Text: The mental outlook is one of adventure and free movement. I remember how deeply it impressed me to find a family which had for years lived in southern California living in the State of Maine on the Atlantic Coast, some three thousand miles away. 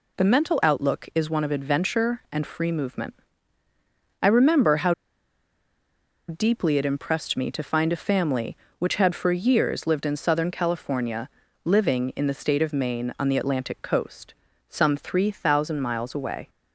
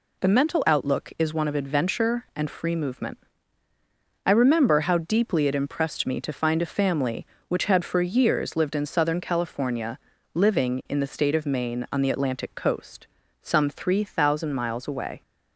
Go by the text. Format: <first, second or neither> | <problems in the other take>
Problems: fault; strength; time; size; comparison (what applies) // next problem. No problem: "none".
second | pauses between "how" and "deeply"; strong; at 4.9 s; 1.3 s long // pauses between "California" and "living"; slight; at 11.2 s; 0.34 s long; slight in the second